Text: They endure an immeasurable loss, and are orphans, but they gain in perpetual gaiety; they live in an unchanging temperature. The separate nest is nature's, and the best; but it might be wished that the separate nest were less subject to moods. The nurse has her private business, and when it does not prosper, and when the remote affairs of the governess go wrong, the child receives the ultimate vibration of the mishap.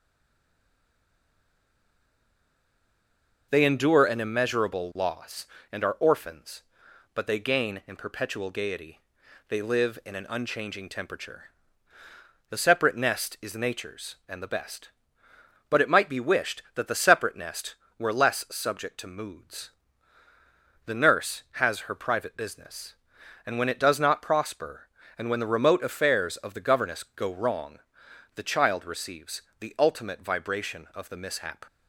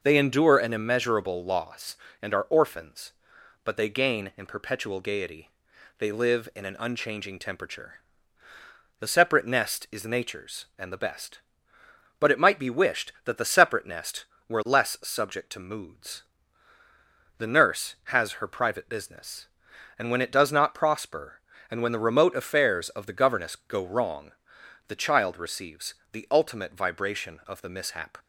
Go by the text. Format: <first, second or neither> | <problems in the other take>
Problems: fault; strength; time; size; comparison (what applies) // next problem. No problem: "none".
second | stays silent before the first word; strong; until 3.4 s; 3.4 s long // pauses between "receives" and "the"; slight; at 29.4 s; 0.18 s long; slight in the second